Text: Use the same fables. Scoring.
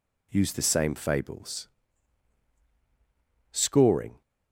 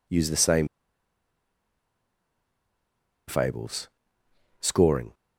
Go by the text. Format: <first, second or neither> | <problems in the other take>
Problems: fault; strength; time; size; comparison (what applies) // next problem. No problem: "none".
first | pauses between "same" and "fables"; strong; at 0.6 s; 2.6 s long